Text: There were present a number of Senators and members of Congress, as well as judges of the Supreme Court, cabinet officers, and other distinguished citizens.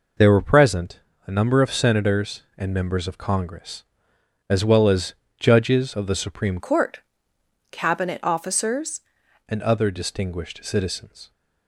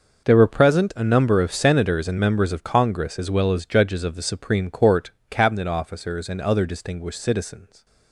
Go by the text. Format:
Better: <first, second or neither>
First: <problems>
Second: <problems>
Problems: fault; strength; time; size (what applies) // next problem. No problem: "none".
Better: second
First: pauses between "present" and "a"; slight; at 0.9 s; 0.30 s long // pauses between "as" and "judges"; slight; at 5.1 s; 0.24 s long // changes voice from "Court" to "officers"; from 6.5 to 8.9 s; 2.4 s long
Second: none